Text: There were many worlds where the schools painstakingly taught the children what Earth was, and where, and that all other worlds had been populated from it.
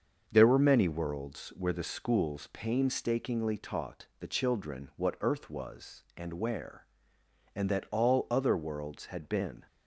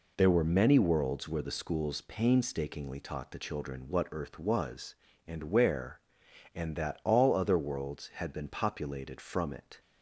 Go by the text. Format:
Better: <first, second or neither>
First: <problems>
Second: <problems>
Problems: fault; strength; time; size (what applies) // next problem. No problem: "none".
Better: second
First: starts louder than the rest; until 1.2 s; 6.5 dB // stops before "populated from it"; at 9.6 s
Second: none